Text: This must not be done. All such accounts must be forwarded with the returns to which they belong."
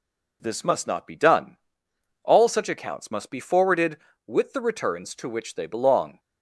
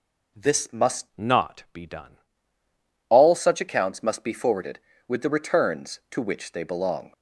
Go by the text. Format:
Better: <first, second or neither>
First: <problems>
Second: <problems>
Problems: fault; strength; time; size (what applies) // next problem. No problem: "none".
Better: first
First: none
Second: changes voice from "not" to "done"; from 1.1 to 2.1 s; 1.0 s long